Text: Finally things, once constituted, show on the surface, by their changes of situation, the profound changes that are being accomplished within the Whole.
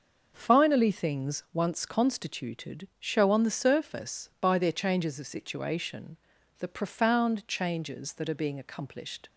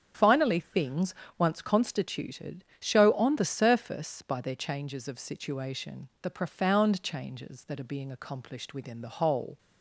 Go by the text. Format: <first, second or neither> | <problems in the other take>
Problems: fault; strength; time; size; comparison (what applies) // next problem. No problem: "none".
second | starts louder than the rest; until 1.3 s; 6 dB; also in the second // stops before "within the Whole"; at 9.2 s